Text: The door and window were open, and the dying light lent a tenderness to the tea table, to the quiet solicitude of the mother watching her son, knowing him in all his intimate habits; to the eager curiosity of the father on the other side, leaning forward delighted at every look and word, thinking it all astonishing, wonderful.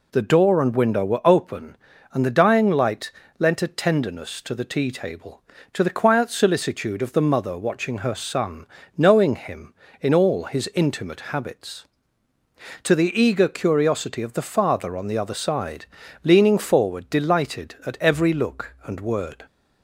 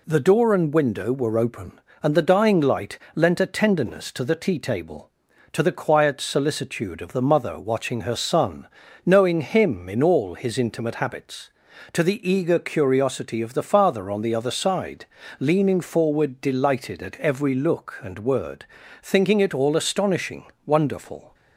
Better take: second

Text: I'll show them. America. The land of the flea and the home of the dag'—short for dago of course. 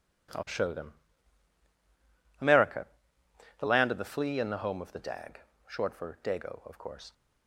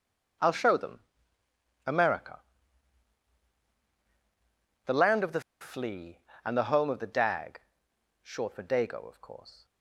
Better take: first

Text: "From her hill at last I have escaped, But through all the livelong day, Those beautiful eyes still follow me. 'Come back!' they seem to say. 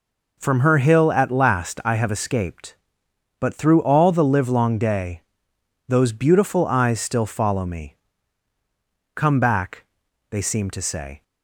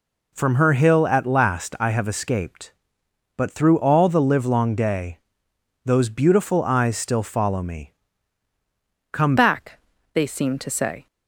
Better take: first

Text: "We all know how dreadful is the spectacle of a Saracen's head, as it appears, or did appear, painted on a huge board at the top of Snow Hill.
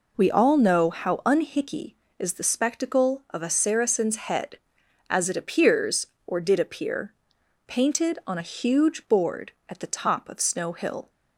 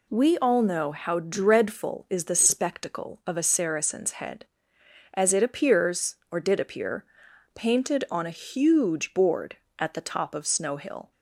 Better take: second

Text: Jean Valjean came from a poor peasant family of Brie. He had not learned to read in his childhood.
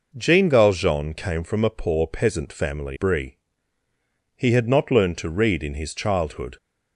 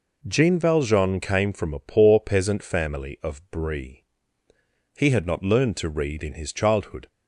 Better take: second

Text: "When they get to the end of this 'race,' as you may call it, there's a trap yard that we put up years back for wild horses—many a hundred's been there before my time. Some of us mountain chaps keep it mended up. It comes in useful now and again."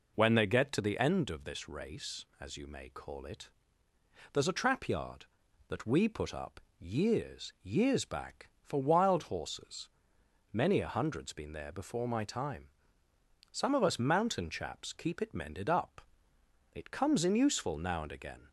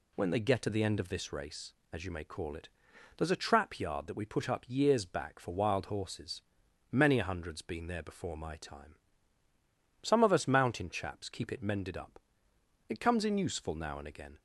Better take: second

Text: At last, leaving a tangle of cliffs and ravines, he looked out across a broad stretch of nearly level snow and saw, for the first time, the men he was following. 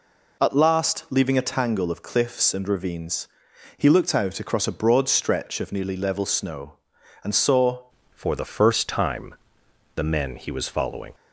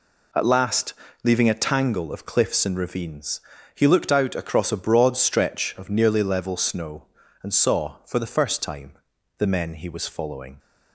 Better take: second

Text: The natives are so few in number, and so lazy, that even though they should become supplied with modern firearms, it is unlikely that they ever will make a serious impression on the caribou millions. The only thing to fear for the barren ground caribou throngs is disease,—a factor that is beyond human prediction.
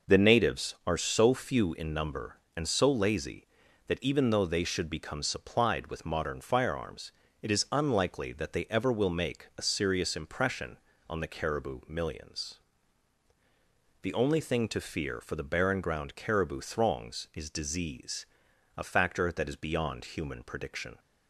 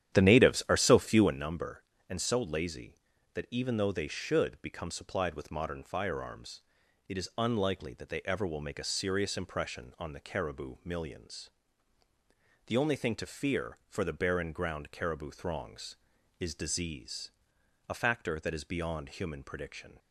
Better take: first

